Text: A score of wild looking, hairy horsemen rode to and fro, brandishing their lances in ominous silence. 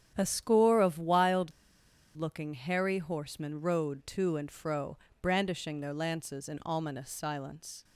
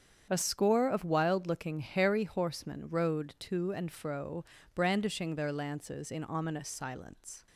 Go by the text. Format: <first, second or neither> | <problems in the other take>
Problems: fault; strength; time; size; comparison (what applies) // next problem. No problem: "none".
second | starts louder than the rest; strong; until 1.1 s; 9 dB; strong in the second // pauses between "wild" and "looking"; noticeable; at 1.5 s; 0.64 s long